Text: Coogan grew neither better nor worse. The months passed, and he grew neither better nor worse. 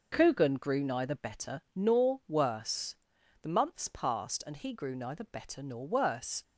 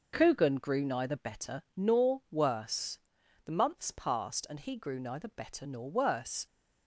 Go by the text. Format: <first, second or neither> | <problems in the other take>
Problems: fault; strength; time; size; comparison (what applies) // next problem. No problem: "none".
neither | none